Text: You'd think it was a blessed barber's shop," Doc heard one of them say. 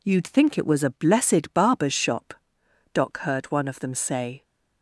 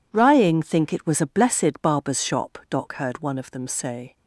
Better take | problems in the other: first | says "Rying" for "You'd"; at 0.1 s

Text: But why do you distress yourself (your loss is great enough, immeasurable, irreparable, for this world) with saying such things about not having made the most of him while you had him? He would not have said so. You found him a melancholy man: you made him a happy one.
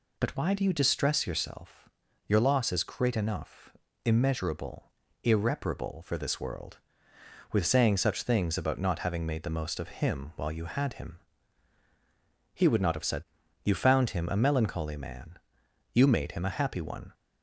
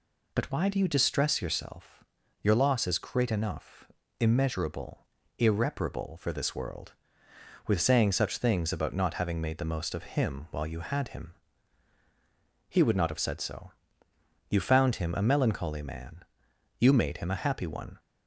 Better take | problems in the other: second | skips "so"; at 13.4 s

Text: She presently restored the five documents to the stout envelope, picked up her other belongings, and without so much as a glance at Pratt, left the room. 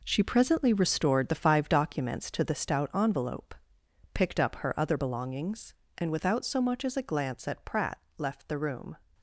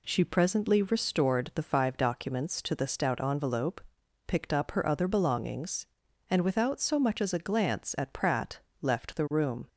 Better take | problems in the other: second | gets quieter; strong; throughout; 9.5 dB

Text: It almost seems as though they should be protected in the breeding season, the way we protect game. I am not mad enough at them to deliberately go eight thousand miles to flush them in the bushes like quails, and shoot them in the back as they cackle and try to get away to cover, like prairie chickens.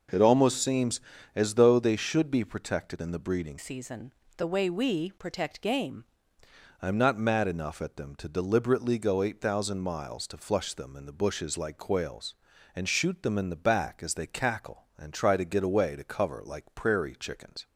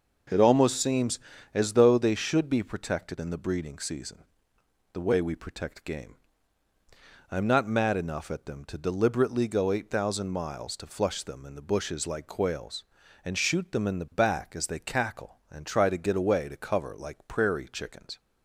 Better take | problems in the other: second | changes voice from "season" to "game"; from 3.5 to 6.0 s; 2.5 s long

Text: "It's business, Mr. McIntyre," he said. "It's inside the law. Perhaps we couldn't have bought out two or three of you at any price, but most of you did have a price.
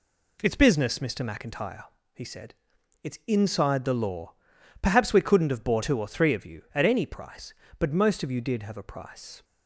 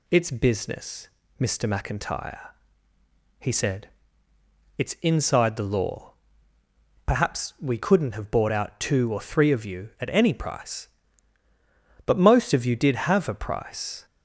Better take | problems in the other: second | skips "out"; at 5.8 s

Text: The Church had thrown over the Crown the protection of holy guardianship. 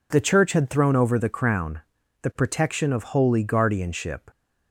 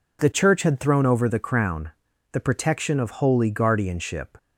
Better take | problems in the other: neither | pauses between "Crown" and "the"; the same in both

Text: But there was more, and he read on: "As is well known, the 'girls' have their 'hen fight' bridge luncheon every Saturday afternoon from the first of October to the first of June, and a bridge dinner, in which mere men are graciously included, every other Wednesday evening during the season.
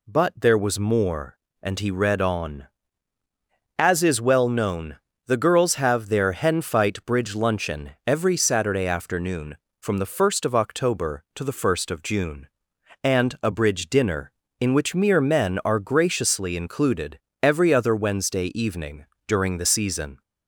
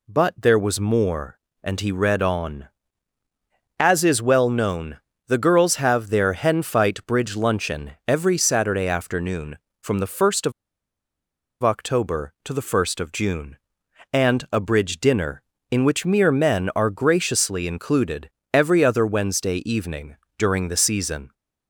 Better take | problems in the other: first | pauses between "of" and "October"; at 10.5 s; 1.1 s long // pauses between "evening" and "during"; slight; at 20.1 s; 0.24 s long; slight in the first

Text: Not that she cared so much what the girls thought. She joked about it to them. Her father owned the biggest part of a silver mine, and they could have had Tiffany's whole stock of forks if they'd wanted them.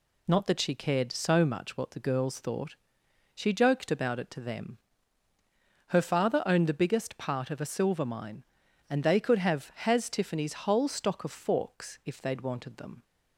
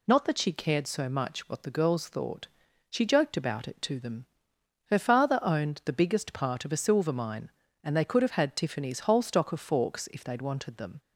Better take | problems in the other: second | says "has" for "had"; at 9.7 s

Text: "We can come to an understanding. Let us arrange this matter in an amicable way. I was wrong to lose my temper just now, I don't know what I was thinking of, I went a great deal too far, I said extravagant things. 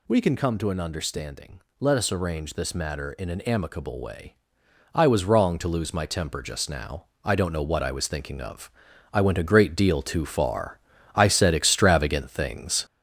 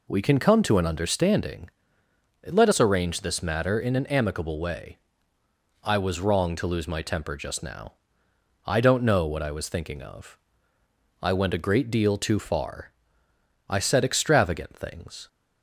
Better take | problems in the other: second | gets louder; noticeable; throughout; 6 dB

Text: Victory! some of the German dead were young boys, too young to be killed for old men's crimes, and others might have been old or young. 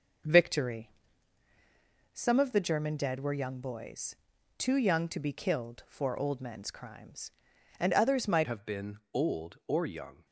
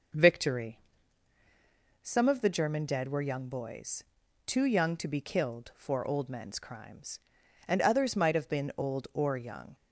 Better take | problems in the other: second | starts louder than the rest; noticeable; until 2.5 s; 6 dB // changes voice at "have"; from 8.4 s on; 1.8 s long

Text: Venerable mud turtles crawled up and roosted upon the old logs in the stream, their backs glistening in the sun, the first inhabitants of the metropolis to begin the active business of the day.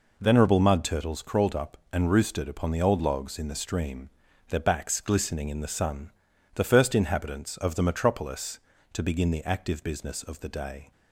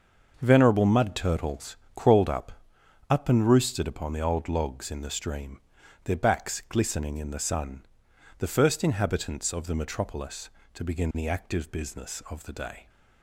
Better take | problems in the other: first | starts louder than the rest; until 1.4 s; 6.5 dB // pauses between "turtles" and "crawled"; slight; at 1.7 s; 0.18 s long // says "up" twice; at 3.0 s

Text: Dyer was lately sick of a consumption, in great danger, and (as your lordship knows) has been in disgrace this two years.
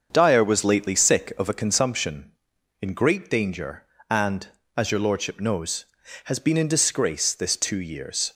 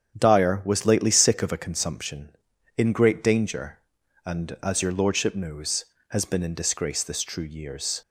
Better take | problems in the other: first | starts louder than the rest; strong; until 1.2 s; 9 dB; also in the first // says "true" for "two"; at 7.2 s

